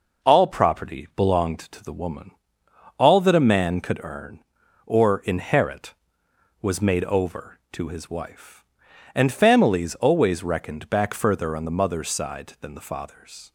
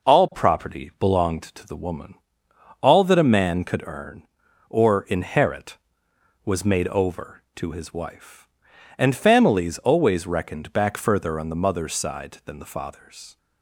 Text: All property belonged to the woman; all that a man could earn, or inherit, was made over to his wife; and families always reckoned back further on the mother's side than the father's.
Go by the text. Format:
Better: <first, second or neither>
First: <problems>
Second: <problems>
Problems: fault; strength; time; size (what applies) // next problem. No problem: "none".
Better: neither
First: none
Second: none